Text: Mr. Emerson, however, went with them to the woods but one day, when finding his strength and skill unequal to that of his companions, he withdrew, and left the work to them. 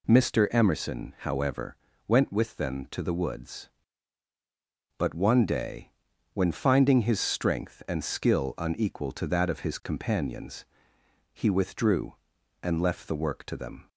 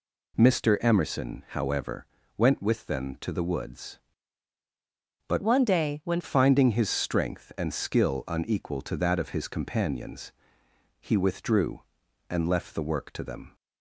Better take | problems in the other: first | changes voice from "one" to "when"; from 5.4 to 6.2 s; 0.8 s long

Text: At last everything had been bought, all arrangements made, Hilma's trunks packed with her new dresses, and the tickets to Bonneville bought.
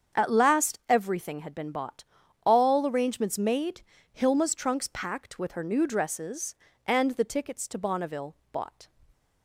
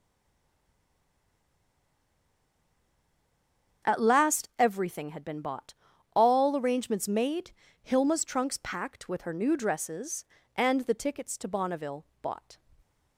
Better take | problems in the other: first | stays silent before the first word; strong; until 3.8 s; 3.8 s long // starts louder than the rest; strong; until 4.9 s; 7.5 dB; strong in the first // pauses between "Bonneville" and "bought"; slight; at 12.0 s; 0.16 s long; slight in the first

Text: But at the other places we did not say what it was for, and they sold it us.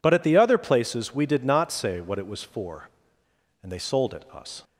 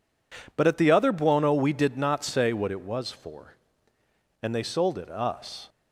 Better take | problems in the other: first | says "buono" for "places"; at 1.1 s

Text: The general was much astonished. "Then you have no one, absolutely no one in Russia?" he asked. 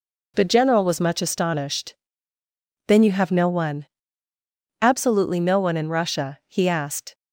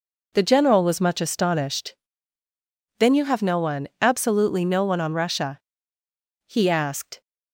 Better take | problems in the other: first | says "on" for "in"; at 5.0 s

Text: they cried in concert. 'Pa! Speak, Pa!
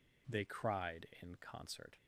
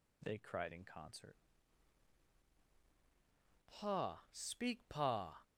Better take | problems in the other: second | stops before "Pa Speak Pa"; at 1.9 s

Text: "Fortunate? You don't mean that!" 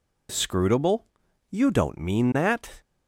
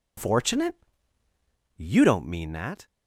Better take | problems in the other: second | says "Scrutable" for "Fortunate"; at 0.3 s

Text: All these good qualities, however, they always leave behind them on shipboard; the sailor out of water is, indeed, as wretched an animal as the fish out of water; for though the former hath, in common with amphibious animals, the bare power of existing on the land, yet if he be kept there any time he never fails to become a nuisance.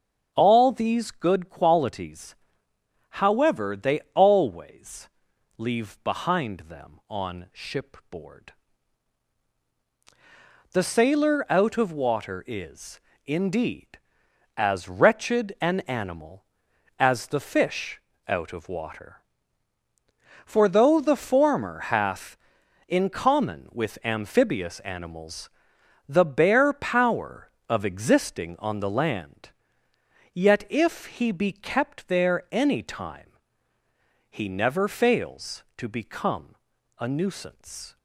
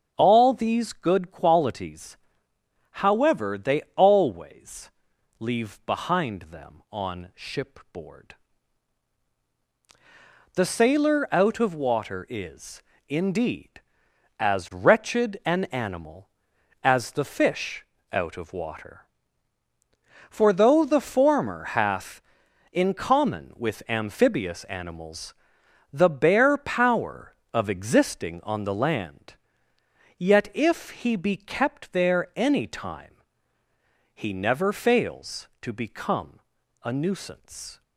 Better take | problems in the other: neither | starts louder than the rest; the same in both // pauses between "always" and "leave"; noticeable; the same in both // pauses between "fish" and "out"; slight; the same in both // pauses between "time" and "he"; the same in both // pauses between "become" and "a"; the same in both

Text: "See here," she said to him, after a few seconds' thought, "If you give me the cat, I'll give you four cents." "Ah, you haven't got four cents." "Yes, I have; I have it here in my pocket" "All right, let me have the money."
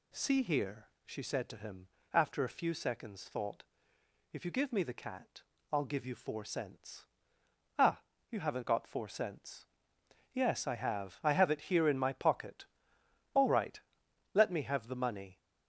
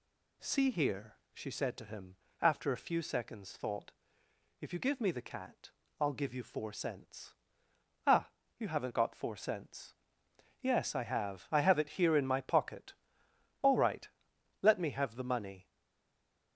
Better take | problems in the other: first | pauses between "pocket" and "All"; noticeable; at 12.9 s; 0.66 s long; noticeable in the first // stays silent after the last word; slight; from 15.6 s on; 0.9 s long

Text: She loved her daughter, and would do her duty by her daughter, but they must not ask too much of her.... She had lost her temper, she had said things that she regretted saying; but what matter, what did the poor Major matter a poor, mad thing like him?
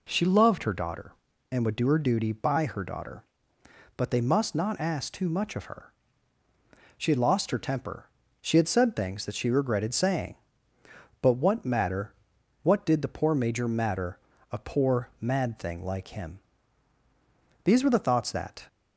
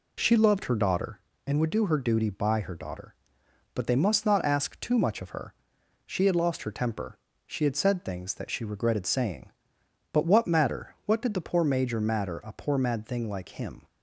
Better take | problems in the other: second | pauses between "matter" and "a"; slight; at 14.1 s; 0.32 s long // goes on to say "These were the thoughts that"; noticeable; from 17.6 s on; 1.0 s long

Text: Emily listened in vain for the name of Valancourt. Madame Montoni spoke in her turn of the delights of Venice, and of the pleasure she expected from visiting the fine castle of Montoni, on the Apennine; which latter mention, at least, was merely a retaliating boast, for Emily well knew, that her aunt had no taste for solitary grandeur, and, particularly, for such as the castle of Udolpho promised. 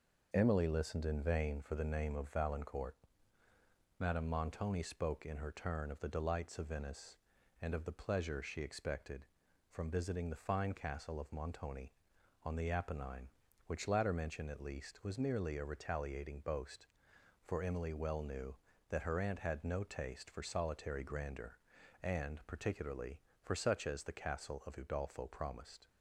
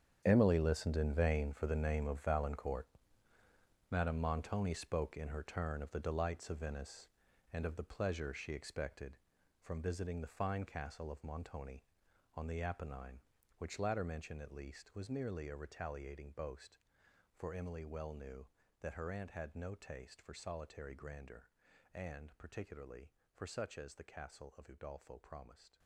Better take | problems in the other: first | gets quieter; strong; throughout; 14.5 dB

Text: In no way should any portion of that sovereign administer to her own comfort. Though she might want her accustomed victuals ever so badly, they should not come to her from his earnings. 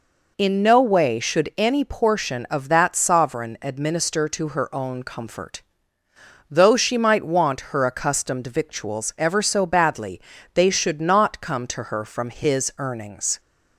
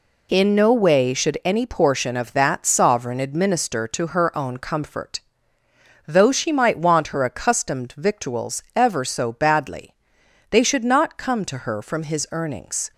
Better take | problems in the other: neither | none

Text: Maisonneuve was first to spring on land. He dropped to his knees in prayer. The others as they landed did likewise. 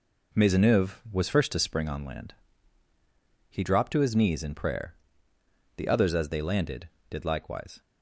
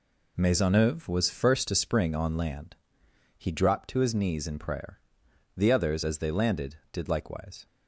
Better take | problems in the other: neither | none

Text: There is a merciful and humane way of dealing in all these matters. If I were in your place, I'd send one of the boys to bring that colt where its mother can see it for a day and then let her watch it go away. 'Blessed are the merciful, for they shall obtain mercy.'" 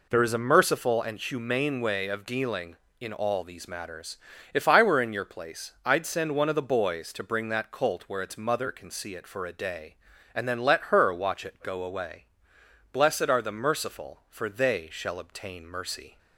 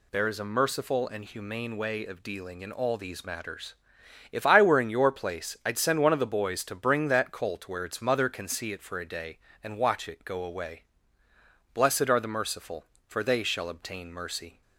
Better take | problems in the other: first | skips "then let her"; at 9.7 s

